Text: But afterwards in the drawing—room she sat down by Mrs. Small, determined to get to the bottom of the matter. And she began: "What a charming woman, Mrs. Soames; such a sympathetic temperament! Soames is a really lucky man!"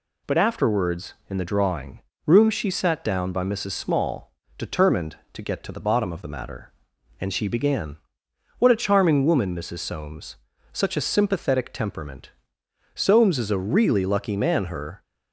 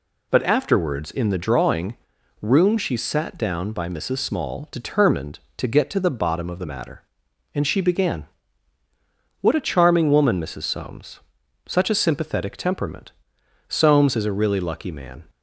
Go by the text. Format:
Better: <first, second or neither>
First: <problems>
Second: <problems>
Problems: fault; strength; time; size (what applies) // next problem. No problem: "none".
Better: second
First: goes on to say "Her"; slight; from 14.6 s on; 0.36 s long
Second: none